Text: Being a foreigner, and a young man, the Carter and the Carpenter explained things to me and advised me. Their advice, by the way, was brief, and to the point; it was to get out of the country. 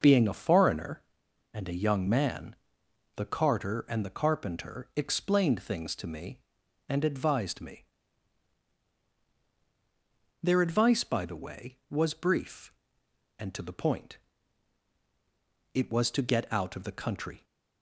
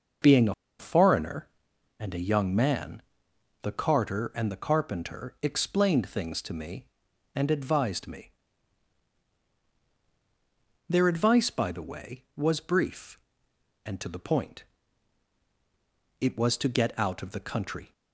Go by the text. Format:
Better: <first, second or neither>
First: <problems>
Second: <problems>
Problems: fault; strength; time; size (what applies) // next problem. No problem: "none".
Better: first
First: none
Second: pauses between "a" and "foreigner"; slight; at 0.5 s; 0.25 s long